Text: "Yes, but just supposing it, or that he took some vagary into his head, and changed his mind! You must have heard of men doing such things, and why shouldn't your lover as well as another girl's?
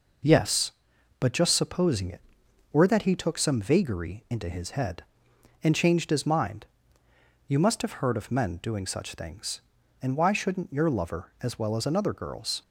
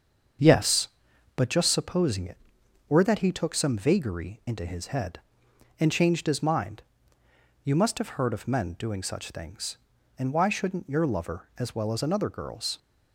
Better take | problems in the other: first | starts louder than the rest; until 1.5 s; 7 dB

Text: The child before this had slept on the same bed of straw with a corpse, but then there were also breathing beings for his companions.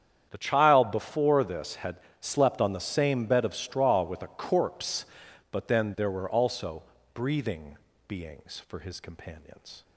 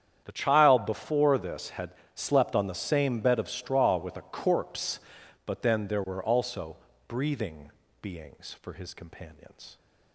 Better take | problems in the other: neither | starts louder than the rest; strong; the same in both // pauses between "had" and "slept"; slight; the same in both // pauses between "also" and "breathing"; slight; the same in both // pauses between "breathing" and "beings"; slight; the same in both

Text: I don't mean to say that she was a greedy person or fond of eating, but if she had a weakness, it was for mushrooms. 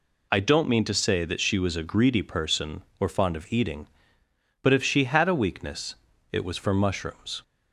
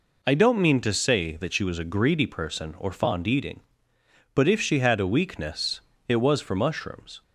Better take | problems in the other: first | skips "of"; at 3.2 s

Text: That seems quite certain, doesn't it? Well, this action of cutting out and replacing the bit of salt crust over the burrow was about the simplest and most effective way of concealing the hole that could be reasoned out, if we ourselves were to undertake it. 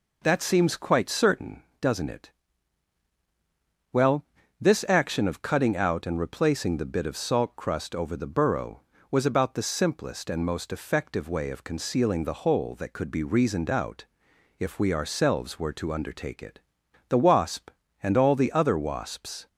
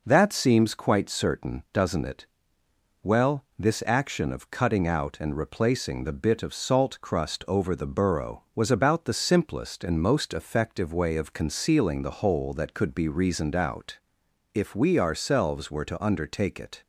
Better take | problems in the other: second | goes on to say "The wasp and all the other wasps"; strong; from 17.0 s on; 2.4 s long

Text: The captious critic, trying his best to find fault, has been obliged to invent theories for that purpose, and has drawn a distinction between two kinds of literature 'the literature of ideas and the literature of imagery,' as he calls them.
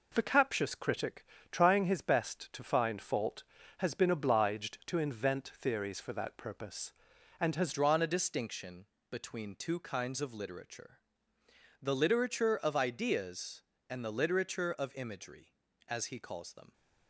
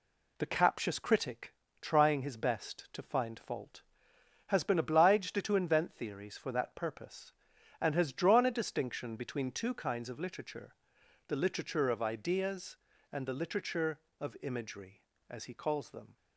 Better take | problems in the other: second | changes voice at "drawn"; from 7.7 s on; 9.0 s long // pauses between "distinction" and "between"; slight; at 8.8 s; 0.24 s long // pauses between "literature" and "the"; noticeable; at 10.9 s; 0.82 s long; noticeable in the second

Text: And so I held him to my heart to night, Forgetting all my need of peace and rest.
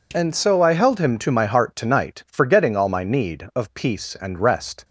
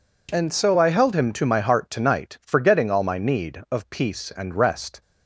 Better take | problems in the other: neither | none

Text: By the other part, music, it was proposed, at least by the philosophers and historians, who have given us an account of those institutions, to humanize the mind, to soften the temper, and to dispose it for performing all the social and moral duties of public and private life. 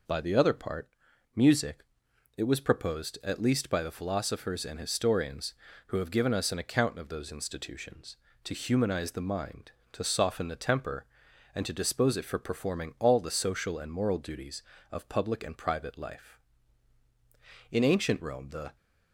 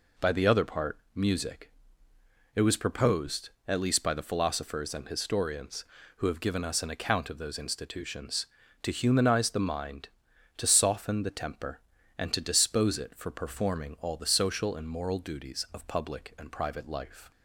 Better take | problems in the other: second | goes on to say "In ancient Rome the"; noticeable; from 17.7 s on; 1.0 s long

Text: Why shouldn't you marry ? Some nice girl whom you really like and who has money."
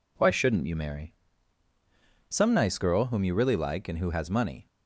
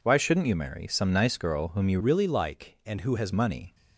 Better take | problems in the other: first | changes voice from "really" to "has"; from 2.0 to 3.3 s; 1.3 s long

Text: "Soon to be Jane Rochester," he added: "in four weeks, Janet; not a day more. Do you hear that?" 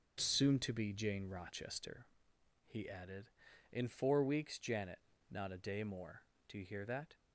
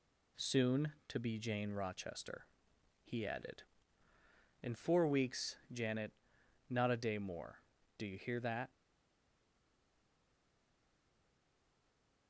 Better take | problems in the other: first | stays silent after the last word; strong; from 8.7 s on; 3.5 s long

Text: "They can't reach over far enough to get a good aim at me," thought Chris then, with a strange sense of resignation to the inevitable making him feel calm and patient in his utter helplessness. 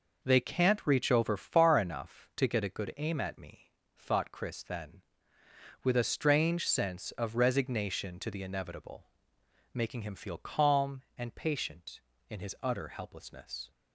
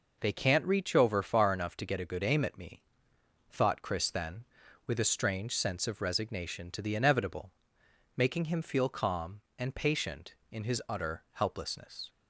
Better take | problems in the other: neither | pauses between "inevitable" and "making"; noticeable; the same in both

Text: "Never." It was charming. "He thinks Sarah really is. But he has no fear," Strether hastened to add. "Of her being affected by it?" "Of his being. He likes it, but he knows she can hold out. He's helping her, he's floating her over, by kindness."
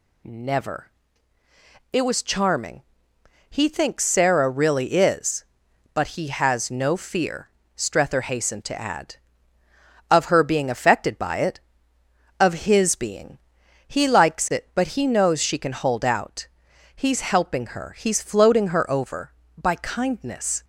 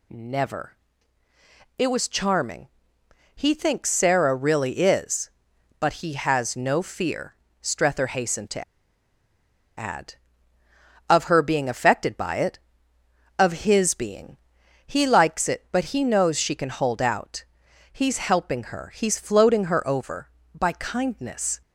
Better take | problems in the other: first | pauses between "to" and "add"; at 8.6 s; 1.1 s long

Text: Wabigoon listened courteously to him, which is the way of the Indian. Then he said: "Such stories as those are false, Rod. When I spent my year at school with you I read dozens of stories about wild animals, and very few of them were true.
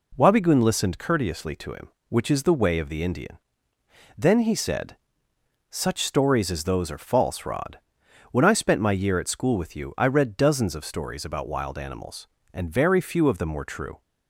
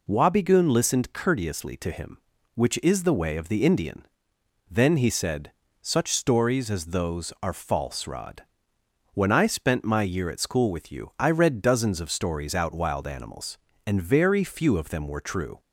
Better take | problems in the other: first | says "out" for "about"; at 12.5 s

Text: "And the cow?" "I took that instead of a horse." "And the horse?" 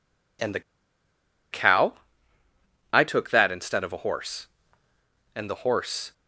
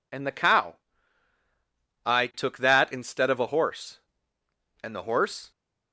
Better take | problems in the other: second | pauses between "the" and "cow"; noticeable; at 0.6 s; 0.91 s long

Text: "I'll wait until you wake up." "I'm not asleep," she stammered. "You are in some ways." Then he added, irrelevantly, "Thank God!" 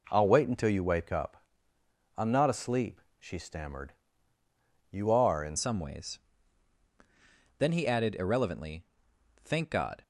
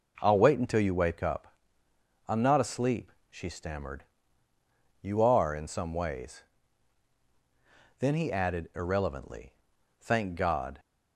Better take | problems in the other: second | changes voice at "some"; from 5.5 s on; 4.5 s long

